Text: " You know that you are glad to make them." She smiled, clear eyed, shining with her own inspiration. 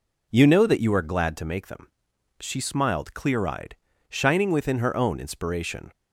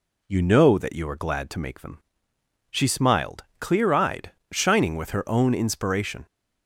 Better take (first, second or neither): second